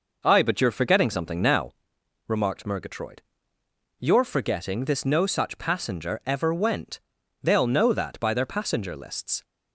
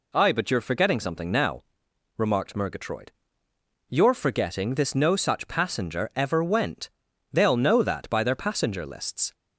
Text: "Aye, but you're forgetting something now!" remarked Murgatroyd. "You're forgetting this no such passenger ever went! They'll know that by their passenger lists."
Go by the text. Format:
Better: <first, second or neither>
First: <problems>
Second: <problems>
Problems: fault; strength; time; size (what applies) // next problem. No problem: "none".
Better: second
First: starts louder than the rest; noticeable; until 1.7 s; 5.5 dB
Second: none